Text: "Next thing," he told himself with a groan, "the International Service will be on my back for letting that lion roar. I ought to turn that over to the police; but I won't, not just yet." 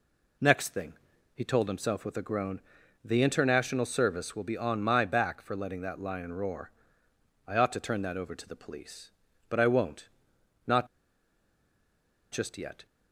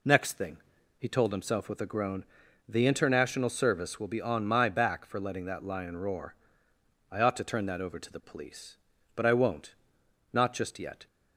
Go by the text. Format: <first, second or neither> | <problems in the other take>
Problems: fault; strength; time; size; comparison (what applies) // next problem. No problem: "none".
second | pauses between "not" and "just"; strong; at 10.8 s; 1.4 s long